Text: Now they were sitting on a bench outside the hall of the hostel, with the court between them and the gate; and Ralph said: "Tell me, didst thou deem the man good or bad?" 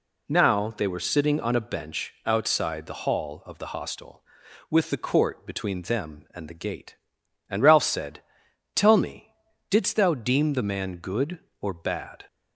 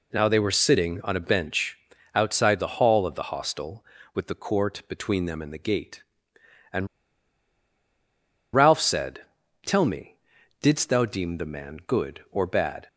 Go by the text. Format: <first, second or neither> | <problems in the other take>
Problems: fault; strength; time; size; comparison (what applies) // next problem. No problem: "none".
first | pauses between "bench" and "outside"; slight; at 1.7 s; 0.36 s long // pauses between "and" and "Ralph"; strong; at 6.8 s; 1.6 s long